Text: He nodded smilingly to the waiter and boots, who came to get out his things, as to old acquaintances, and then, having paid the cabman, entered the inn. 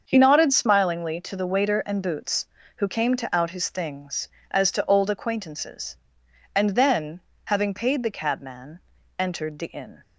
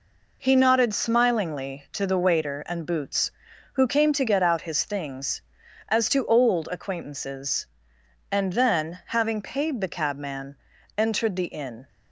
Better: second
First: starts louder than the rest; until 1.0 s; 7 dB // skips "get"; at 3.3 s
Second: none

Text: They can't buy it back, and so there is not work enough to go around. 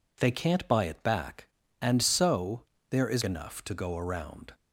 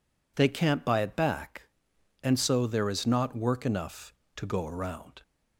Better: second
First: pauses between "so" and "there"; slight; at 2.6 s; 0.28 s long // skips "not work"; at 3.2 s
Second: none

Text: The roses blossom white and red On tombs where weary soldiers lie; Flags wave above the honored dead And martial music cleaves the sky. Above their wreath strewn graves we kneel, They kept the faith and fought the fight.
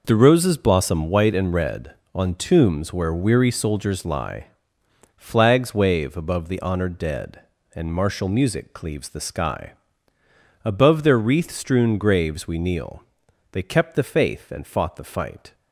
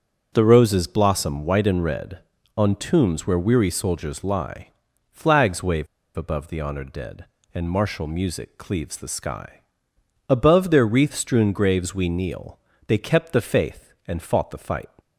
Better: first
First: none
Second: starts louder than the rest; until 1.3 s; 7 dB // pauses between "wave" and "above"; slight; at 5.8 s; 0.28 s long

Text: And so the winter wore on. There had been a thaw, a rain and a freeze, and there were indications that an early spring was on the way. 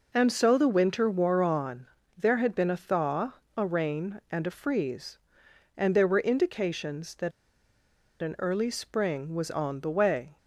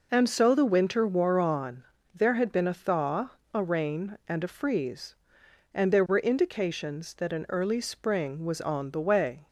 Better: second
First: pauses between "that" and "an"; noticeable; at 7.3 s; 0.91 s long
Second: none

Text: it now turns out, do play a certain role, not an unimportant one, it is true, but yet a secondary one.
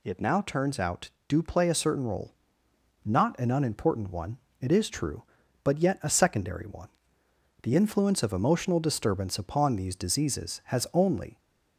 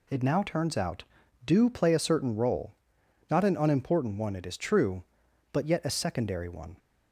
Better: second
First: goes on to say "The influence of emotional disturbance upon these diseases has only"; strong; from 7.6 s on; 3.7 s long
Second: none

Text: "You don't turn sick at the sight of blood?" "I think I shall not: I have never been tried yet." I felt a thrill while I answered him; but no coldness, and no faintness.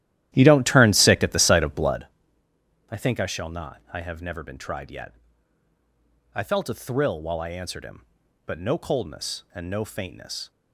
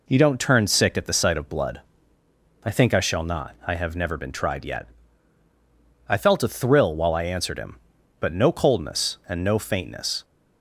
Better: second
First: starts louder than the rest; strong; until 2.1 s; 13 dB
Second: none

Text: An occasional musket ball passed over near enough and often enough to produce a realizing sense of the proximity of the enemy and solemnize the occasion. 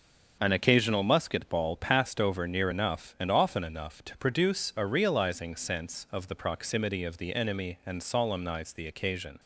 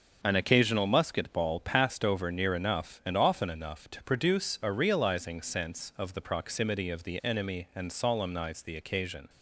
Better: neither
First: starts louder than the rest; until 1.4 s; 6.5 dB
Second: starts louder than the rest; until 1.2 s; 6.5 dB

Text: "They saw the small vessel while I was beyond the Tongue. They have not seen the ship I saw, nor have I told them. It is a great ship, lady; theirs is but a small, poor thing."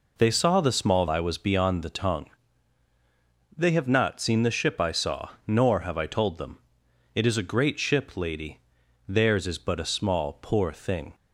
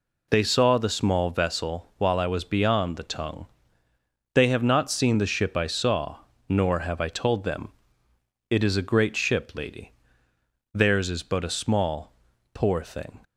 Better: second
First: skips "vessel while"; at 1.0 s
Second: none

